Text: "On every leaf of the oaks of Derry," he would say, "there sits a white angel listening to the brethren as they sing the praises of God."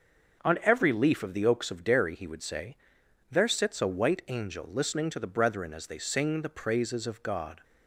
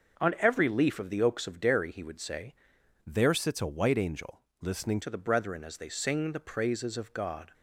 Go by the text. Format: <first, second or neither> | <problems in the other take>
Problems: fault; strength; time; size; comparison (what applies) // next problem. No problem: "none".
first | starts louder than the rest; noticeable; until 1.2 s; 6 dB; noticeable in the first // changes voice from "there" to "listening"; from 3.0 to 5.0 s; 2.0 s long // pauses between "angel" and "listening"; slight; at 4.4 s; 0.18 s long